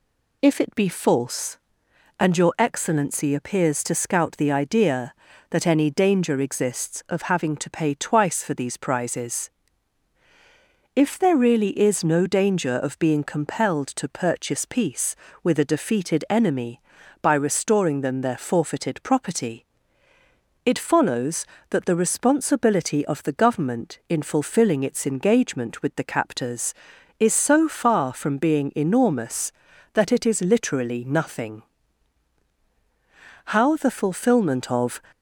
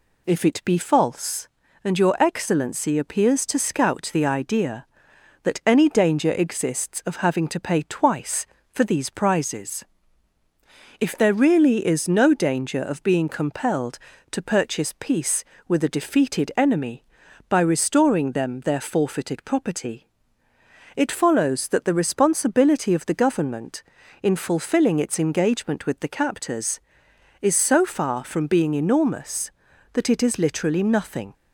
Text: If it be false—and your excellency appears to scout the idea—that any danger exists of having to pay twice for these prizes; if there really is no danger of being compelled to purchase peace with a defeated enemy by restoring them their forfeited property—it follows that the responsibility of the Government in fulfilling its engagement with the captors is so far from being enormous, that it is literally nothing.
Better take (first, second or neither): second